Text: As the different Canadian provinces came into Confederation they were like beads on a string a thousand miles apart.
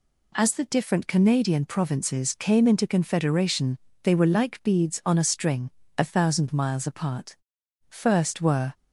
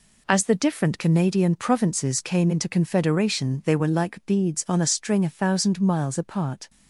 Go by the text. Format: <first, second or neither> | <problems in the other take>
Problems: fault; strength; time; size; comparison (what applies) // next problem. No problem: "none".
second | pauses between "Confederation" and "they"; slight; at 3.7 s; 0.24 s long // pauses between "string" and "a"; slight; at 5.6 s; 0.26 s long // goes on to say "First were"; noticeable; from 7.8 s on; 0.84 s long